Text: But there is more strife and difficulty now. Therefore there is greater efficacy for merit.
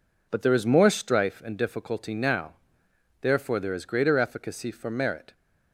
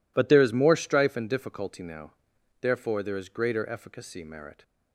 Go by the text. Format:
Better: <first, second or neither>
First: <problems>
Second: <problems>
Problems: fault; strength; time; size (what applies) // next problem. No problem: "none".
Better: first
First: none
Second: skips "for"; at 4.2 s